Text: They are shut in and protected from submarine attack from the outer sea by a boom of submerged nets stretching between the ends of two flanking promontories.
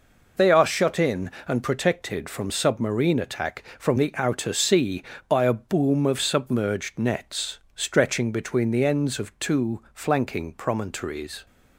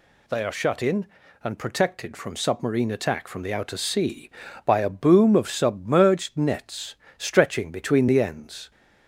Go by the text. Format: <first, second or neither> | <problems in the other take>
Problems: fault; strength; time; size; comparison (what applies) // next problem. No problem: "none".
first | pauses between "nets" and "stretching"; slight; at 6.9 s; 0.22 s long; slight in the first // stops before "of two flanking promontories"; at 8.7 s